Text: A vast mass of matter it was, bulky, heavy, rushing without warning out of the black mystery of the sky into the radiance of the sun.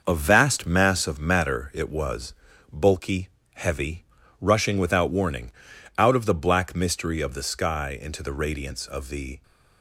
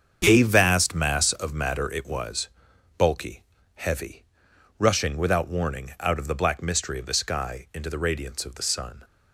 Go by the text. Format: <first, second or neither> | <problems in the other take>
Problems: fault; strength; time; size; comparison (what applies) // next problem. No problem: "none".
second | starts louder than the rest; until 1.0 s; 6 dB; strong in the second // pauses between "warning" and "out"; at 5.5 s; 0.44 s long // stops before "sun"; at 9.4 s